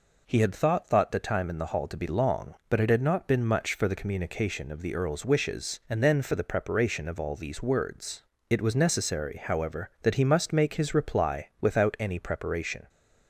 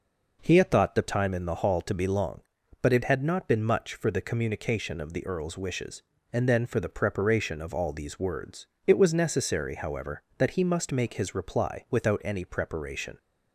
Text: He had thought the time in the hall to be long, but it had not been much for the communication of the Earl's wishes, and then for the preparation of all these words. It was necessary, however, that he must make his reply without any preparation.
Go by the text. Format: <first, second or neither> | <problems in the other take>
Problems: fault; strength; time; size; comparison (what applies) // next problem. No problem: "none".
second | says "thought" twice; at 0.8 s